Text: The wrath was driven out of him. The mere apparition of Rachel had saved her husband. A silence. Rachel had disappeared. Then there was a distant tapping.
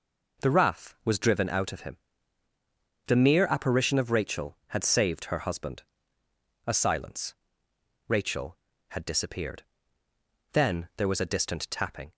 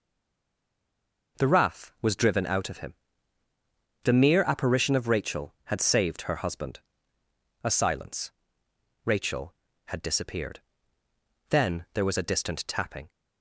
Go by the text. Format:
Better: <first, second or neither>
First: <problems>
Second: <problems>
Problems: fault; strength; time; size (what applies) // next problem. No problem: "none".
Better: first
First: none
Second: stays silent before the first word; noticeable; until 1.3 s; 1.3 s long